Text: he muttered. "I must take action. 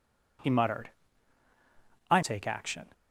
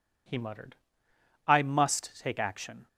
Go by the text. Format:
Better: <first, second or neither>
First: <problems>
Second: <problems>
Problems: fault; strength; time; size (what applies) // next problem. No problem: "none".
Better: second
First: skips "must"; at 2.2 s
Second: none